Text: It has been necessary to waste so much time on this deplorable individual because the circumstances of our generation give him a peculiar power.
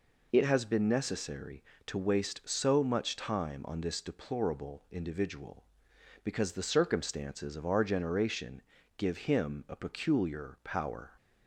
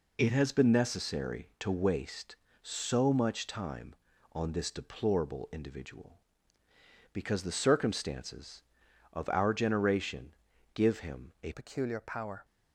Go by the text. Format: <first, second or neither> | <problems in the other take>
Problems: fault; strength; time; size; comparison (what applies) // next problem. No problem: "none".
first | pauses between "generation" and "give"; at 10.3 s; 0.42 s long; slight in the first // changes voice at "peculiar"; from 11.5 s on; 0.9 s long